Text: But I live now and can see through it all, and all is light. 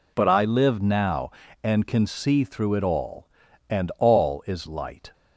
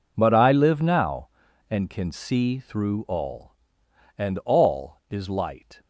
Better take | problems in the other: first | skips "it"; at 3.0 s

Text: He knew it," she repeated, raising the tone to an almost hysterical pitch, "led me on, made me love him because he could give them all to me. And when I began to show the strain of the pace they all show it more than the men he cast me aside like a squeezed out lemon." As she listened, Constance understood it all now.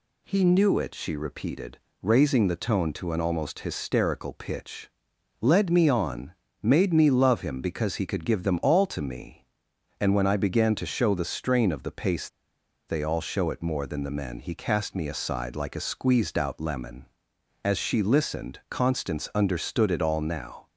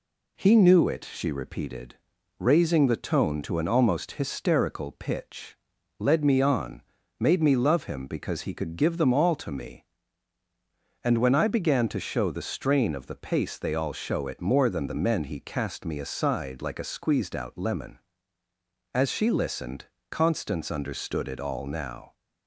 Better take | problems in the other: second | pauses between "pace" and "they"; noticeable; at 12.2 s; 0.61 s long

